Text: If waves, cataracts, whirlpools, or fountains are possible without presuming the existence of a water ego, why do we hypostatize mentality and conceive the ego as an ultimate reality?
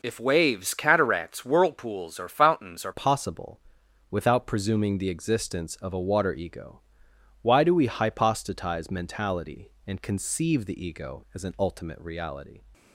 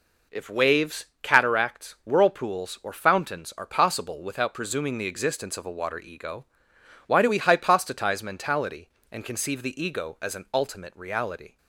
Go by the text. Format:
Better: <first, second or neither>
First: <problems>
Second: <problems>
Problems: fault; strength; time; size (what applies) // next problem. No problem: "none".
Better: second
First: changes voice at "possible"; from 2.9 s on; 9.7 s long // pauses between "possible" and "without"; noticeable; at 3.6 s; 0.50 s long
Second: none